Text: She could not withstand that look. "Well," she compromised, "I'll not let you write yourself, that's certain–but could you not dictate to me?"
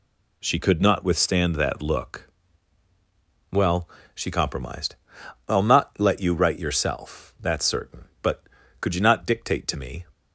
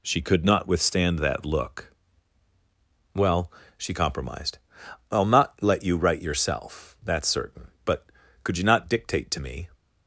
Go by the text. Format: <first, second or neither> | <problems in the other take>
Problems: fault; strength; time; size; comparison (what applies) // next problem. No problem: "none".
neither | none